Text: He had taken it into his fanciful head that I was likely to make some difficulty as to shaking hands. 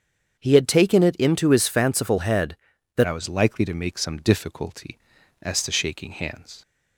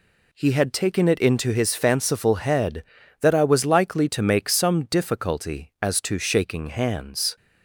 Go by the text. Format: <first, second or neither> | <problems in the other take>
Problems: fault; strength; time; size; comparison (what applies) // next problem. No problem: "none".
second | starts louder than the rest; strong; until 1.4 s; 7.5 dB // changes voice at "I"; from 3.0 s on; 3.6 s long